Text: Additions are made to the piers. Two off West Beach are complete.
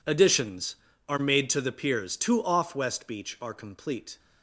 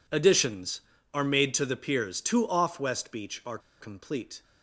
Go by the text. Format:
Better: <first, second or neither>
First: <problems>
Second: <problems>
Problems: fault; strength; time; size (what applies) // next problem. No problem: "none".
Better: first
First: none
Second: pauses between "are" and "complete"; slight; at 3.5 s; 0.21 s long